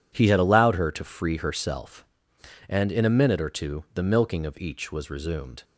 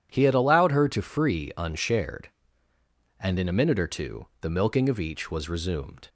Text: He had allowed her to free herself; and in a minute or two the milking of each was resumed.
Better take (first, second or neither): first